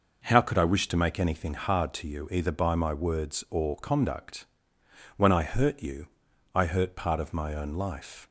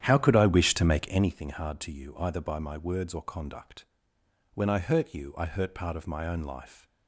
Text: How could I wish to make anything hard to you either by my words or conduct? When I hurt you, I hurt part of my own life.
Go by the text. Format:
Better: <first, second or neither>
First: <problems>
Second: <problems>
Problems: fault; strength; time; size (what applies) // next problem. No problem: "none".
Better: first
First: none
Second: starts louder than the rest; strong; until 1.4 s; 10 dB